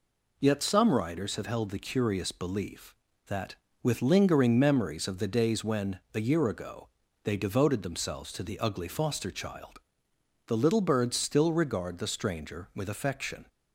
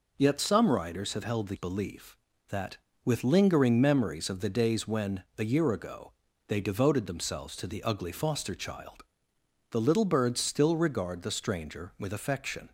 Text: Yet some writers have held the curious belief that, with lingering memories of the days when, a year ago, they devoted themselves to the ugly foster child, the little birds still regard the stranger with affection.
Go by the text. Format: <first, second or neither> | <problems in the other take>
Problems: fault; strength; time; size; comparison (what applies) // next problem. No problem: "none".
first | skips "curious"; at 1.5 s